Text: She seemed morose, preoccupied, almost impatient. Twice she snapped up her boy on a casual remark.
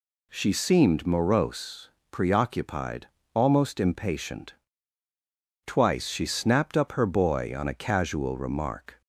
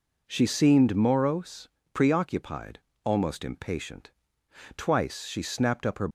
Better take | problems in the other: first | stops before "boy on a casual remark"; at 6.0 s

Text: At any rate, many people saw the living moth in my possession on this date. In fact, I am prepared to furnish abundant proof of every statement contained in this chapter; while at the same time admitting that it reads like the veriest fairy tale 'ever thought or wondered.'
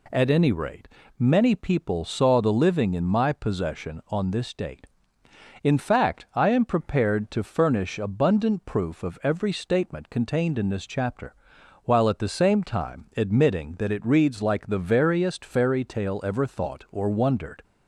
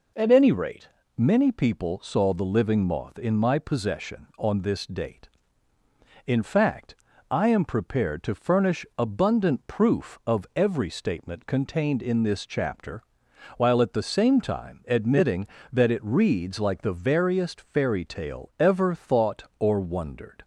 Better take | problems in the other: second | skips "moth"; at 2.9 s

